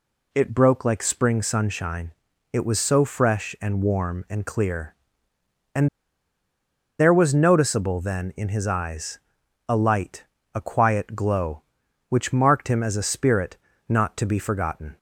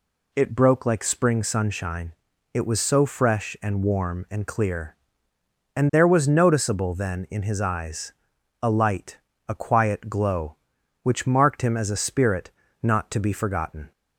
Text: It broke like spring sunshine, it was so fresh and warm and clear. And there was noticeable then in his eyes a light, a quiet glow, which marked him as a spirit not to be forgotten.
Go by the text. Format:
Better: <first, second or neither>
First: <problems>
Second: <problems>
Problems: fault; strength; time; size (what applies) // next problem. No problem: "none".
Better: second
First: pauses between "And" and "there"; at 5.8 s; 1.1 s long // pauses between "eyes" and "a"; noticeable; at 9.1 s; 0.50 s long // pauses between "spirit" and "not"; slight; at 13.5 s; 0.30 s long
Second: pauses between "eyes" and "a"; noticeable; at 8.1 s; 0.50 s long // pauses between "spirit" and "not"; slight; at 12.5 s; 0.30 s long